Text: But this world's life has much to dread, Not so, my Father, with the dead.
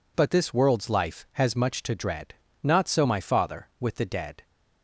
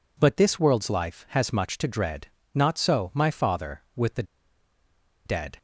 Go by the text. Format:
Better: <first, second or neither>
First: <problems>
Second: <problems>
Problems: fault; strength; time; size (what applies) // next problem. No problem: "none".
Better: first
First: none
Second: pauses between "the" and "dead"; at 4.2 s; 1.0 s long